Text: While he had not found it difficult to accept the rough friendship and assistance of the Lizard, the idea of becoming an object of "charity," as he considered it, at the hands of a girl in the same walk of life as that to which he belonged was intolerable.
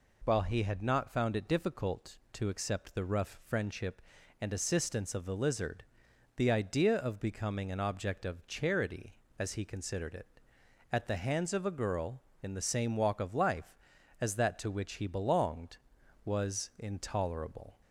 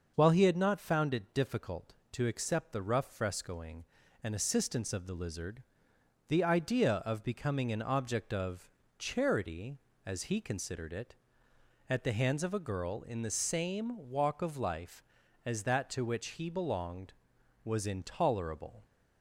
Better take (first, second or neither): first